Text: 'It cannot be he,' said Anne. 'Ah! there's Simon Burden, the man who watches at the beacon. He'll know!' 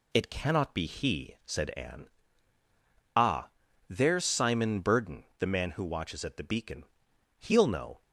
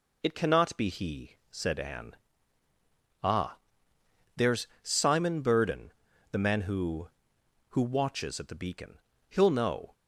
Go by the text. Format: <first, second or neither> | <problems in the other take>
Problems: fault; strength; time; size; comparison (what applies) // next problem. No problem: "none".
first | pauses between "there's" and "Simon"; slight; at 4.6 s; 0.16 s long // says "who" twice; at 7.6 s